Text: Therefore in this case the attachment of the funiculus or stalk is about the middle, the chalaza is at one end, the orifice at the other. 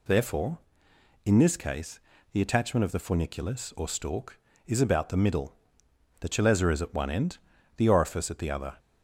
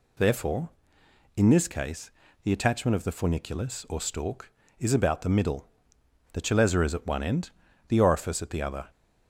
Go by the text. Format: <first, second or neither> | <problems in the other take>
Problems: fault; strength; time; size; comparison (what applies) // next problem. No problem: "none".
neither | pauses between "case" and "the"; slight; the same in both